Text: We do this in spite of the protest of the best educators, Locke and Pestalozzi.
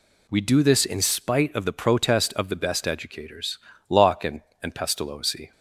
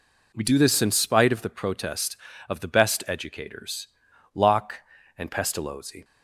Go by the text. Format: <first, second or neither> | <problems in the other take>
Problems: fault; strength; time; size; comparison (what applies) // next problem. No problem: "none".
second | says "and" twice; at 4.6 s